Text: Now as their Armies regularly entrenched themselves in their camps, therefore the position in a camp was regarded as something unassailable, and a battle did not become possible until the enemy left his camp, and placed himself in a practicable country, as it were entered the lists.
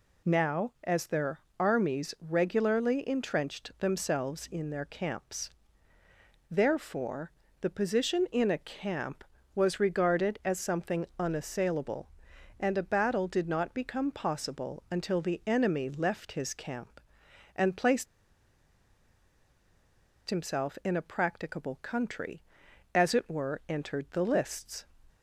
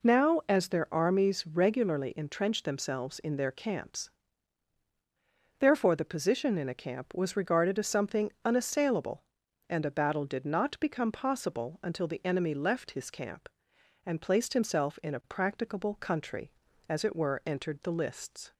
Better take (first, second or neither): second